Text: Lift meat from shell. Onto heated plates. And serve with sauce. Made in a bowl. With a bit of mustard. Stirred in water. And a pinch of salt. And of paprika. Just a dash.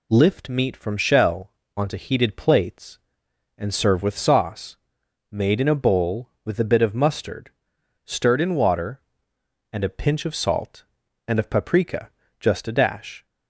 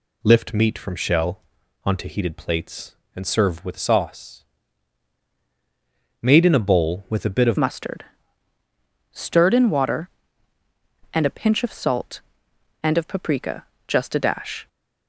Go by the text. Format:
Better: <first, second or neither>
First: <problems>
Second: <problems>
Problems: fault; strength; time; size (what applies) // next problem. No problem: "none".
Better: first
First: none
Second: changes voice at "mustard"; from 7.5 s on; 7.1 s long